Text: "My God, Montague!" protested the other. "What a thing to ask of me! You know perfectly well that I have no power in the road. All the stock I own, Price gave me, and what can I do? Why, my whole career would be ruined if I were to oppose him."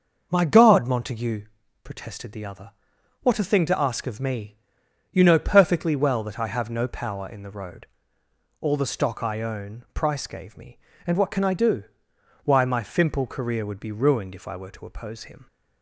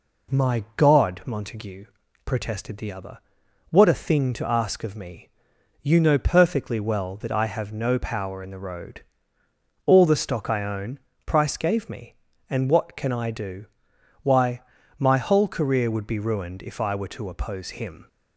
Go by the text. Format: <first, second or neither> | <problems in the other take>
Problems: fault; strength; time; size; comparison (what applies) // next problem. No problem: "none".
second | starts louder than the rest; until 1.3 s; 6 dB // says "fimple" for "whole"; at 12.8 s